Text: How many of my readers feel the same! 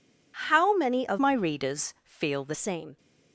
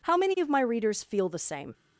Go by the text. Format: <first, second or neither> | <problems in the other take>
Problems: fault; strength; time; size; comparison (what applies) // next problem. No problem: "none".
second | changes voice from "my" to "the"; from 1.1 to 2.5 s; 1.4 s long